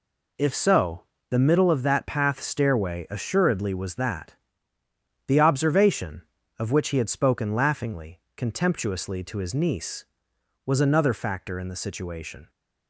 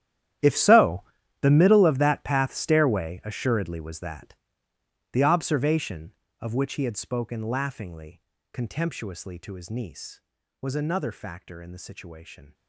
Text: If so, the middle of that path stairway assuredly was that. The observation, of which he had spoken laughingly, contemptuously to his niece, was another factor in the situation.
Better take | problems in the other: first | gets quieter; strong; throughout; 18 dB

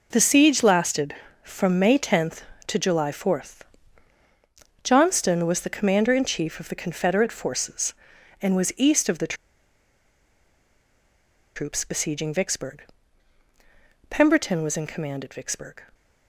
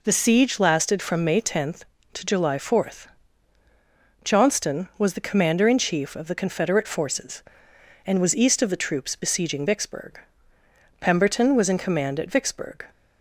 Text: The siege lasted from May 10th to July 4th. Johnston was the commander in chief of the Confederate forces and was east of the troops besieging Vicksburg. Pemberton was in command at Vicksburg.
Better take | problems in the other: second | pauses between "the" and "troops"; strong; at 9.3 s; 2.2 s long

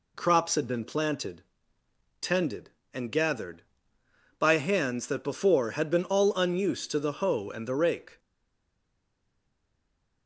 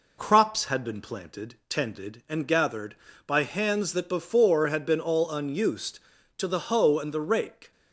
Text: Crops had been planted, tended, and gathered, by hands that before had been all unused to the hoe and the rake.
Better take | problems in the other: second | stays silent after the last word; noticeable; from 8.1 s on; 2.1 s long

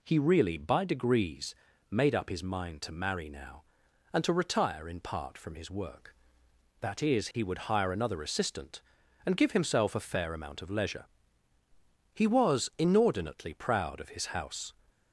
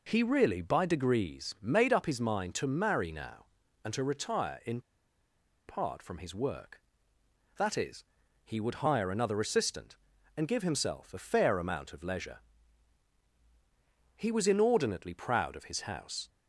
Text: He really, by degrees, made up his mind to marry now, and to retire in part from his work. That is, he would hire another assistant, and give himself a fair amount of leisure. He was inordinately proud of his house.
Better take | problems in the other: first | pauses between "in" and "part"; noticeable; at 4.7 s; 0.87 s long

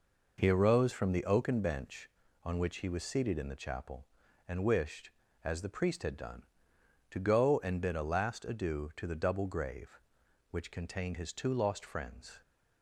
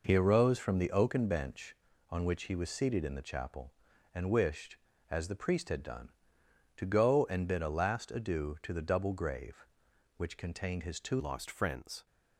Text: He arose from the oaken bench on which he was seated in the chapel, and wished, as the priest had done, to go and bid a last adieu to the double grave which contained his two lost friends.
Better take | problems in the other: first | changes voice at "lost"; from 11.1 s on; 0.9 s long

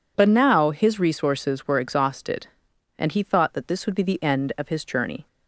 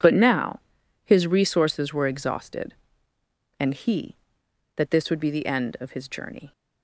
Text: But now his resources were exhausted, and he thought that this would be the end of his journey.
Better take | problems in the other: first | pauses between "now" and "his"; noticeable; at 0.5 s; 0.46 s long // skips "thought"; at 4.4 s

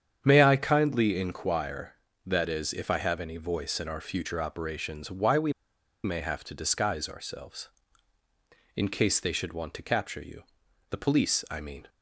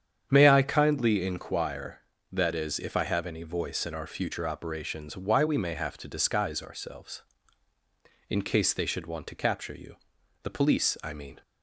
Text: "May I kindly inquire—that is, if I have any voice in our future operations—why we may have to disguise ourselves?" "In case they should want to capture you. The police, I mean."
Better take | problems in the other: second | starts louder than the rest; strong; until 1.2 s; 8.5 dB; strong in the second // pauses between "we" and "may"; noticeable; at 5.5 s; 0.52 s long

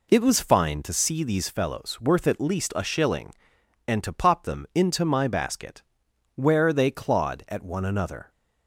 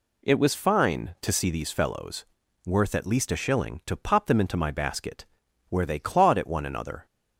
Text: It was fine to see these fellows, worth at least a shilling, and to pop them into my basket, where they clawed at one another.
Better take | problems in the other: first | skips "and"; at 3.8 s

